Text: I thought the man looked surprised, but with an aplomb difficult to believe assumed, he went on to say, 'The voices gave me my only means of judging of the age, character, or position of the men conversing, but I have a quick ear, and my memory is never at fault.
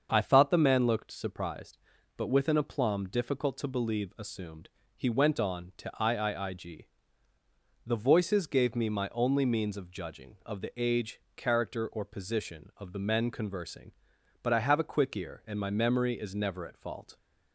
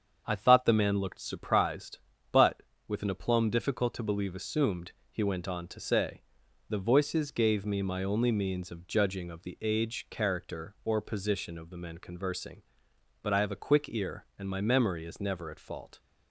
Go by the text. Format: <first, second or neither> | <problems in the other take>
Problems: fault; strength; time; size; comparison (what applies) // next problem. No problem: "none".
second | starts louder than the rest; until 1.1 s; 7 dB; strong in the second // says "iiig" for "say"; at 6.0 s